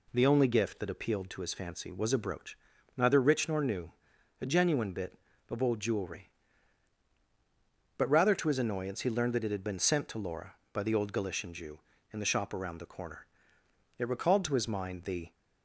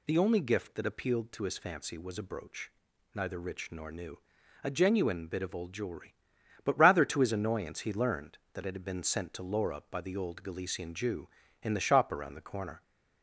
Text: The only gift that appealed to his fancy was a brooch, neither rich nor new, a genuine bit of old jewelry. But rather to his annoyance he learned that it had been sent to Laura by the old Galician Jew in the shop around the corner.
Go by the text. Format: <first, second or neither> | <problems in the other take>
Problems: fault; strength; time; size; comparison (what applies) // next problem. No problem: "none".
second | goes on to say "It recalled to his mind the"; from 13.9 s on; 1.3 s long